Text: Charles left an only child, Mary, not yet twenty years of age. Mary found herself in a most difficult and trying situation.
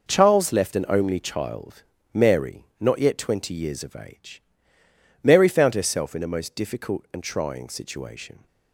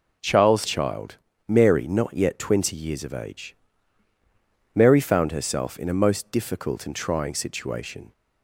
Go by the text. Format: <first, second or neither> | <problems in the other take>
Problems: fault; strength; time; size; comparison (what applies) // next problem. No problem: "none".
first | skips "left an only"; at 0.6 s